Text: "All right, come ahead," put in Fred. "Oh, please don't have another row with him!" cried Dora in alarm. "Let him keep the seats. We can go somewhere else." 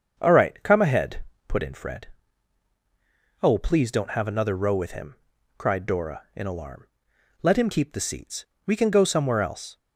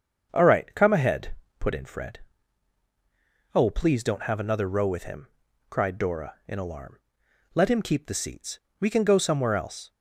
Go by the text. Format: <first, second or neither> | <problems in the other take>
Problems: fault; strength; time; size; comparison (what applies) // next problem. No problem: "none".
neither | starts louder than the rest; the same in both